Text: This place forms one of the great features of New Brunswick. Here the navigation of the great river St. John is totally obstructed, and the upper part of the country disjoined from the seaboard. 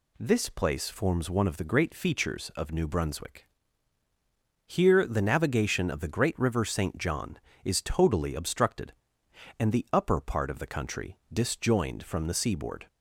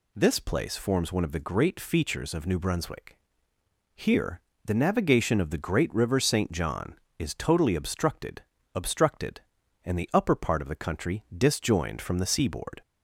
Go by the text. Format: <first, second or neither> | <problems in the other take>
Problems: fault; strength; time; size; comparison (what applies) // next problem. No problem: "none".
first | pauses between "Here" and "the"; slight; at 4.4 s; 0.24 s long // says "obstructed" twice; at 8.7 s